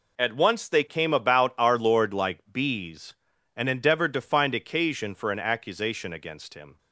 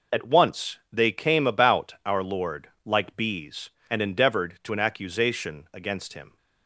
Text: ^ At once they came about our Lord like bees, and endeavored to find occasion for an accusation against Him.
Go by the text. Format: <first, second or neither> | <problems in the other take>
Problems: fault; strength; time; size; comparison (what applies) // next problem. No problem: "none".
first | pauses between "Lord" and "like"; slight; at 2.6 s; 0.16 s long // skips "find occasion for"; at 4.7 s